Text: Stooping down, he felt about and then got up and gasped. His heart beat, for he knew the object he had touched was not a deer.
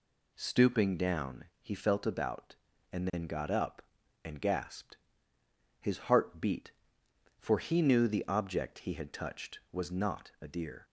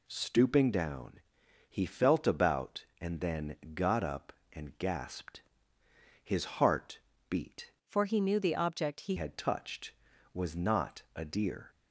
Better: first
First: none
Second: pauses between "then" and "got"; slight; at 3.5 s; 0.18 s long // pauses between "heart" and "beat"; slight; at 6.9 s; 0.28 s long // changes voice from "for" to "he"; from 7.8 to 9.1 s; 1.3 s long

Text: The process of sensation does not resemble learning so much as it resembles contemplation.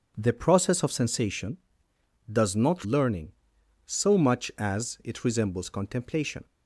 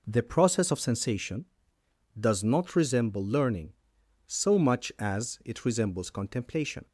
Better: second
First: skips "resemble"; at 2.8 s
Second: none

